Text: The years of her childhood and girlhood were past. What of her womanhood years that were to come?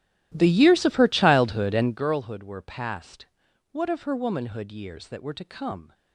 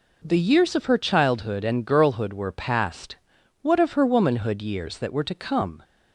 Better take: second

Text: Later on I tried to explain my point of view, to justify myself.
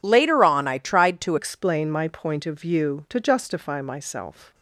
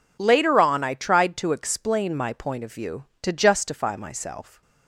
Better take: second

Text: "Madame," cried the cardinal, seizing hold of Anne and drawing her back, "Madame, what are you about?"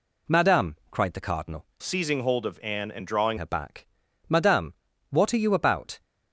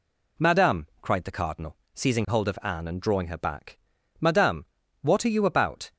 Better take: second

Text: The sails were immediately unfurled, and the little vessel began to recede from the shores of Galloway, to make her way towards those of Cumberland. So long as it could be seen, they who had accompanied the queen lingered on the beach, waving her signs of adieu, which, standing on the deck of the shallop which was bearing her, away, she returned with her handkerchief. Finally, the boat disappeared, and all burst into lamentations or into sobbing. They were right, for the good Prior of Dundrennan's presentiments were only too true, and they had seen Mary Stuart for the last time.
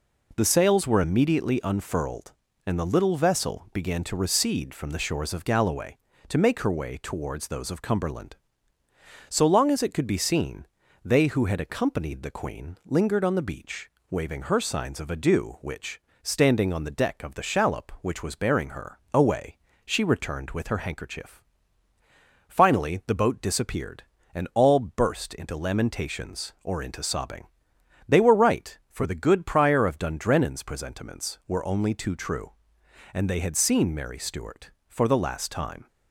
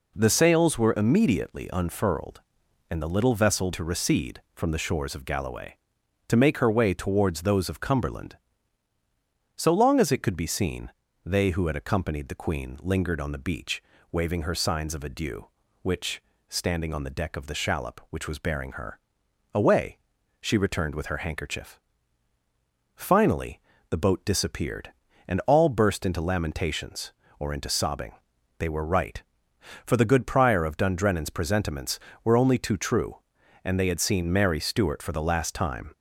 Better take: first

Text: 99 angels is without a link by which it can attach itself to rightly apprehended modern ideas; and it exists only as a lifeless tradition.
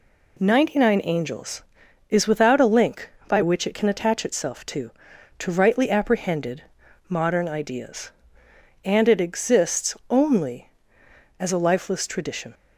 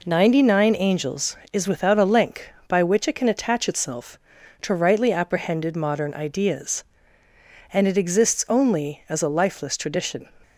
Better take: second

